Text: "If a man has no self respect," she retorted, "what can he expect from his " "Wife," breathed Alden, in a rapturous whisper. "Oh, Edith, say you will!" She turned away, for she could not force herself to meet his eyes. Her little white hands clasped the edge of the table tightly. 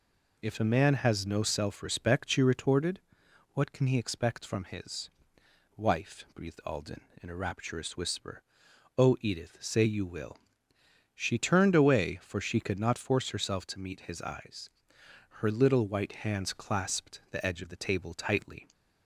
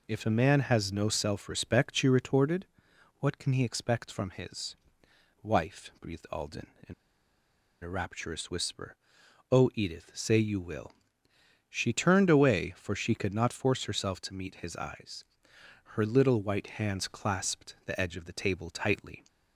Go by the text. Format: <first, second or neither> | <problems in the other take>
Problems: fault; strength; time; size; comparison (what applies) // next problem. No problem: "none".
first | pauses between "in" and "a"; noticeable; at 6.9 s; 0.89 s long